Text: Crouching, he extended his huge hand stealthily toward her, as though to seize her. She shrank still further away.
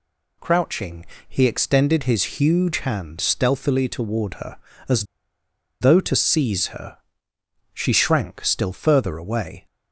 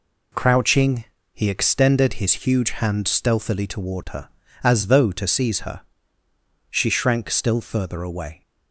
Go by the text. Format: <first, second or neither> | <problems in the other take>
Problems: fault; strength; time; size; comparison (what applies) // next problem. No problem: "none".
second | pauses between "as" and "though"; noticeable; at 5.0 s; 0.76 s long